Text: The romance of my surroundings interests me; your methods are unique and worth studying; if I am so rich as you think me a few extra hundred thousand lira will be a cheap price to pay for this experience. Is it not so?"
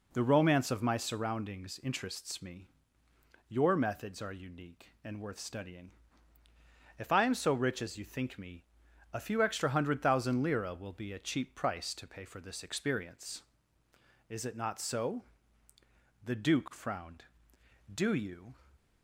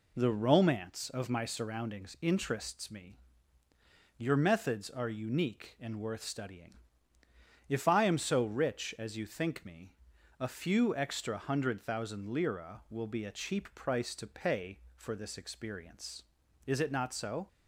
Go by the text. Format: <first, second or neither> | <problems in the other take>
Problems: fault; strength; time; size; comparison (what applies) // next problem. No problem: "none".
second | pauses between "me" and "a"; noticeable; at 8.6 s; 0.48 s long; noticeable in the second // goes on to say "The Duke frowned Do you"; strong; from 16.2 s on; 2.3 s long